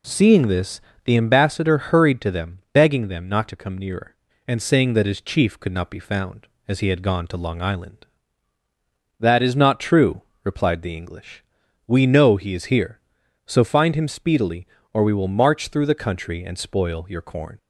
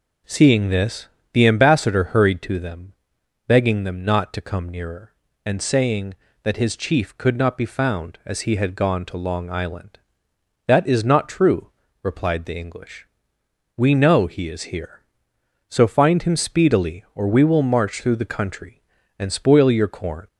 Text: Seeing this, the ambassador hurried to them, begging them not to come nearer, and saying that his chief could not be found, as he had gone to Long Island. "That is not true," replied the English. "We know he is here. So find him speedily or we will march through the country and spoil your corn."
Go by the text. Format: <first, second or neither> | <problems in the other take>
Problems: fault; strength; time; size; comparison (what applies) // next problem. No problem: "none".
neither | none